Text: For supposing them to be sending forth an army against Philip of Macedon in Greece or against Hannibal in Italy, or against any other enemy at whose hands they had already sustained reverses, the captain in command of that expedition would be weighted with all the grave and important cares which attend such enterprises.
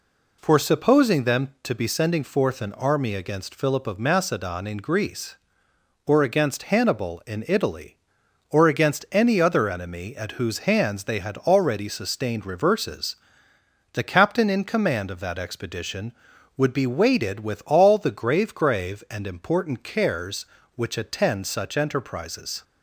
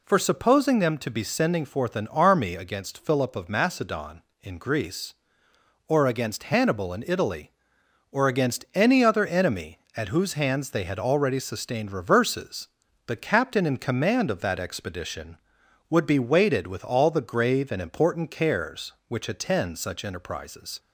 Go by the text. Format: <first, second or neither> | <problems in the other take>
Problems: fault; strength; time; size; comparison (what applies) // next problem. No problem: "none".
second | says "grave" twice; at 18.5 s